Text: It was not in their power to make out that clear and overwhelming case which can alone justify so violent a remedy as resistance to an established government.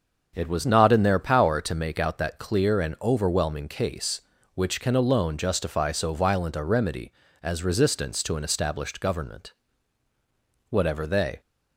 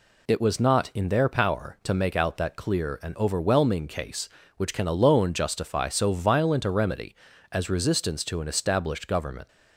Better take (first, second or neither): second